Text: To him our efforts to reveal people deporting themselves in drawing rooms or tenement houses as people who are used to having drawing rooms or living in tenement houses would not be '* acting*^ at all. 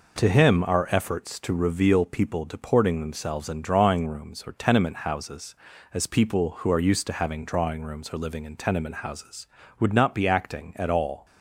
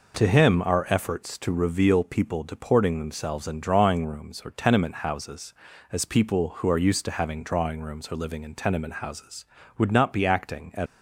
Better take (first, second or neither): first